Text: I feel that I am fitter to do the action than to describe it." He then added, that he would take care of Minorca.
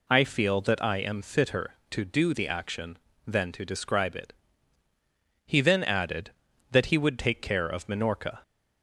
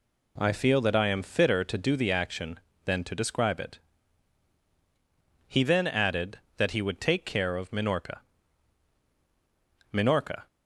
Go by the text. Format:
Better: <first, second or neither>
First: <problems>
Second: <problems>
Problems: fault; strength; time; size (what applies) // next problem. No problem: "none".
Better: first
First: none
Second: says "Minorca" twice; at 9.9 s